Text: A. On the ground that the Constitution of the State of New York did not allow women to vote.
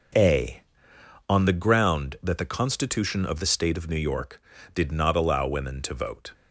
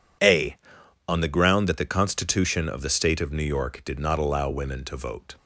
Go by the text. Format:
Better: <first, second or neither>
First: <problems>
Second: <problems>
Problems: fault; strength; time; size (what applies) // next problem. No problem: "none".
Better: neither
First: none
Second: none